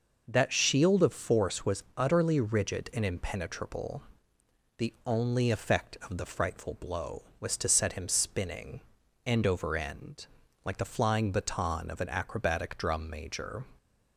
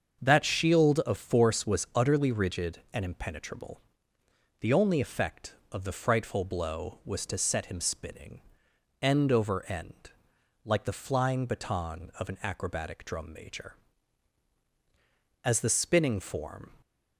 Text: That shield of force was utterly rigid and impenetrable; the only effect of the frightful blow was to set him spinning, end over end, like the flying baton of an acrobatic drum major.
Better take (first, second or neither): first